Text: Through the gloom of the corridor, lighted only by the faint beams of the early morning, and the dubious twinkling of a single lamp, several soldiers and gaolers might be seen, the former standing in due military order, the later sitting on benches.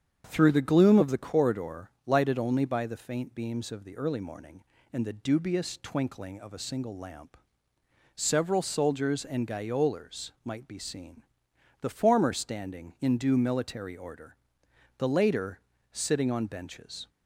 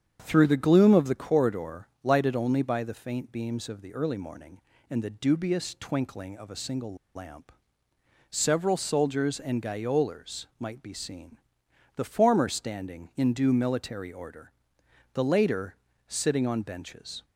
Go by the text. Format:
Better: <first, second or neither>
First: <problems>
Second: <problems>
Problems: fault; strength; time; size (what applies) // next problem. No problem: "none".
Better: first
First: starts louder than the rest; strong; until 1.2 s; 8 dB // pauses between "later" and "sitting"; slight; at 15.5 s; 0.32 s long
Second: starts louder than the rest; strong; until 1.2 s; 8 dB // pauses between "single" and "lamp"; slight; at 6.9 s; 0.20 s long // pauses between "later" and "sitting"; slight; at 15.7 s; 0.32 s long